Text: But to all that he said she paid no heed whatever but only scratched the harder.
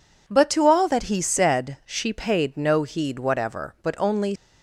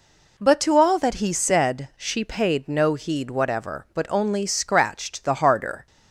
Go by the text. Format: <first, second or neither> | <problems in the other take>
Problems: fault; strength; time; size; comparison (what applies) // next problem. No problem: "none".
second | stops before "scratched the harder"; at 4.3 s